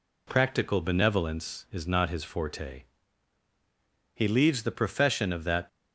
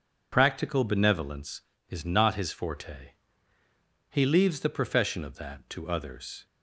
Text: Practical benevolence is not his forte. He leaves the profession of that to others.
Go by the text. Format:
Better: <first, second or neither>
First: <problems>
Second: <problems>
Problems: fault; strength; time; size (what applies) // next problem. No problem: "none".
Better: second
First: stops before "to others"; at 5.6 s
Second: none